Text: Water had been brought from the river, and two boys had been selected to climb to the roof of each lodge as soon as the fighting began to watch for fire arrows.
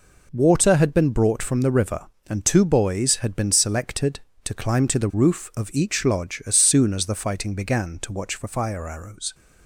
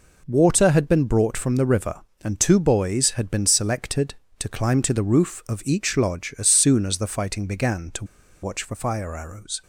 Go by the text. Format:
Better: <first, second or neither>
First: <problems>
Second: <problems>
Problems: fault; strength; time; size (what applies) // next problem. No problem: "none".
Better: first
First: none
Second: pauses between "to" and "watch"; at 8.0 s; 0.37 s long